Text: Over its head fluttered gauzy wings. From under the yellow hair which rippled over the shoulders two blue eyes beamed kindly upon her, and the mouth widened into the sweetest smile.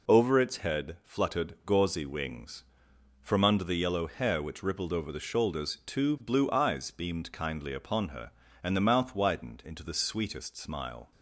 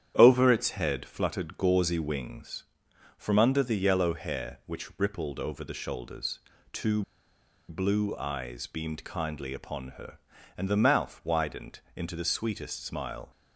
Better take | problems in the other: first | starts louder than the rest; strong; until 1.1 s; 9.5 dB // pauses between "shoulders" and "two"; slight; at 6.3 s; 0.32 s long // pauses between "two" and "blue"; noticeable; at 7.0 s; 0.67 s long

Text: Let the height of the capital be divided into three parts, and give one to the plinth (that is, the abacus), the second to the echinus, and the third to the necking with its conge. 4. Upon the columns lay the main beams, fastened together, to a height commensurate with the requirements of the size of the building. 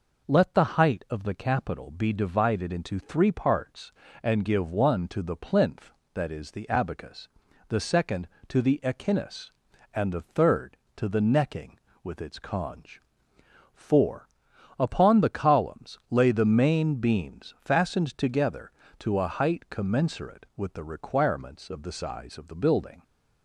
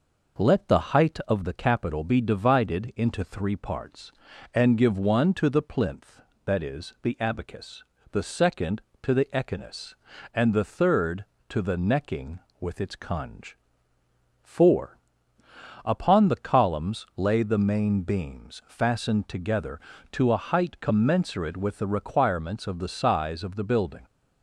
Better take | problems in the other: neither | none

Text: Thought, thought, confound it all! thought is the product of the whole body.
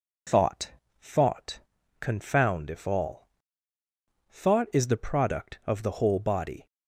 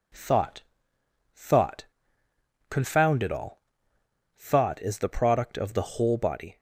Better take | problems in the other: second | says "if" for "it"; at 2.6 s

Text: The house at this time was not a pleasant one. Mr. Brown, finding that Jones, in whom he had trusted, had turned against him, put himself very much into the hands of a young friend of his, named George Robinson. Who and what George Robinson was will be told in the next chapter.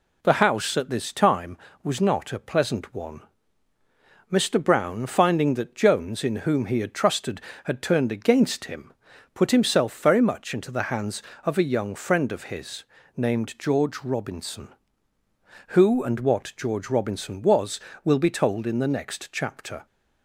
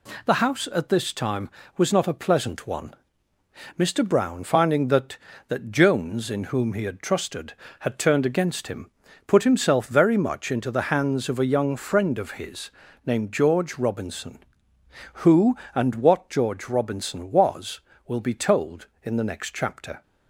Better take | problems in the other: first | says "that" twice; at 5.4 s

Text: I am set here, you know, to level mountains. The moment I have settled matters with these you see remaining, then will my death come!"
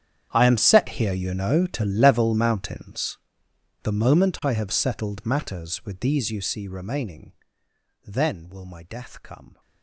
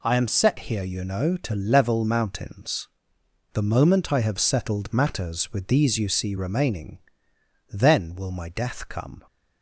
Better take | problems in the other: second | gets quieter; strong; throughout; 19.5 dB

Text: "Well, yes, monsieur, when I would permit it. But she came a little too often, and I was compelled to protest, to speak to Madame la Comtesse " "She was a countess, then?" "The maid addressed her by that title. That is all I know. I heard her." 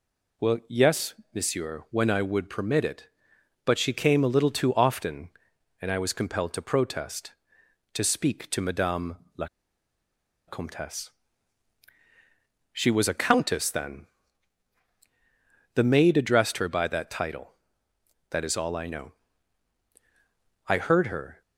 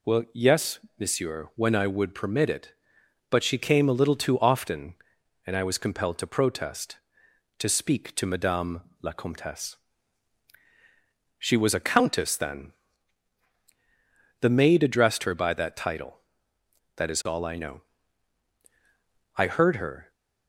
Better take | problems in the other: second | pauses between "Madame" and "la"; slight; at 9.1 s; 0.20 s long; slight in the second // pauses between "la" and "Comtesse"; at 9.4 s; 1.0 s long

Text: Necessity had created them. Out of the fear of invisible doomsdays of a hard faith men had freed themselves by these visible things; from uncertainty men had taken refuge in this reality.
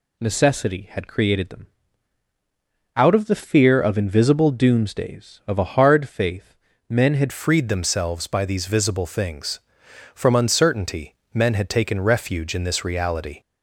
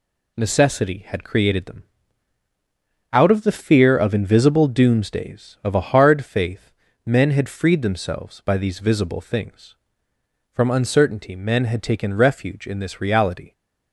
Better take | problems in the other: second | pauses between "faith" and "men"; slight; at 6.5 s; 0.34 s long; slight in the second // changes voice at "freed"; from 7.3 s on; 6.1 s long // pauses between "uncertainty" and "men"; slight; at 11.1 s; 0.18 s long

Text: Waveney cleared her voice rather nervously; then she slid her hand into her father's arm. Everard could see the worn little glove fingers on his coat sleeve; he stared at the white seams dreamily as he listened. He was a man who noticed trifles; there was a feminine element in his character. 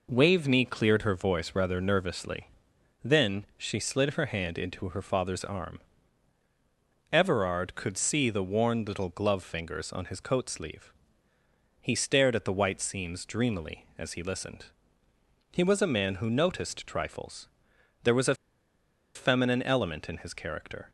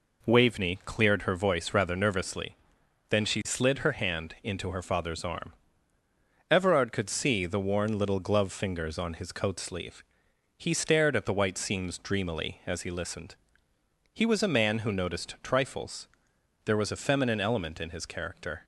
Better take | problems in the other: second | pauses between "a" and "feminine"; noticeable; at 18.3 s; 0.81 s long

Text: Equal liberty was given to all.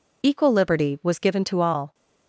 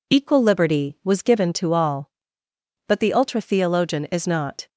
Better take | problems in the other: first | goes on to say "But the ultra theologian is not"; strong; from 2.8 s on; 1.8 s long

